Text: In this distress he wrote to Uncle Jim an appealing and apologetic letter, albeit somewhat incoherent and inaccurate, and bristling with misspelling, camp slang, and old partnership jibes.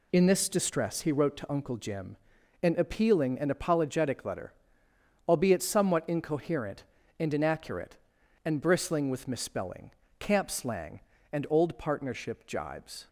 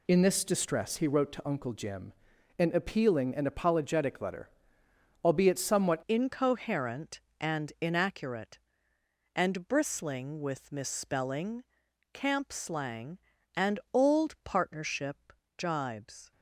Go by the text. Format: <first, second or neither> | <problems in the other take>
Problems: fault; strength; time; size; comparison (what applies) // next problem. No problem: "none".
first | pauses between "Jim" and "an"; noticeable; at 2.1 s; 0.46 s long; noticeable in the first // changes voice at "incoherent"; from 6.0 s on; 10.3 s long // pauses between "and" and "old"; slight; at 13.7 s; 0.16 s long // pauses between "partnership" and "jibes"; slight; at 15.3 s; 0.24 s long